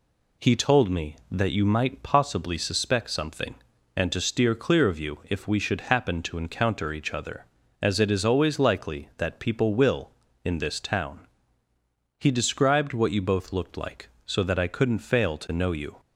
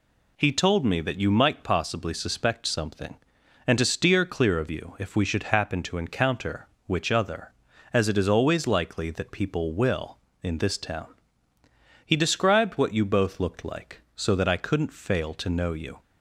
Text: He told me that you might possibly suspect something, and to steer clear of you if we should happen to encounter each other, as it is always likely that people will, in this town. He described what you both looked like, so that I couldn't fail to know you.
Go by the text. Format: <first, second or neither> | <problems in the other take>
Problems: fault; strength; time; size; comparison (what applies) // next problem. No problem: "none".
first | says "which" for "each"; at 6.8 s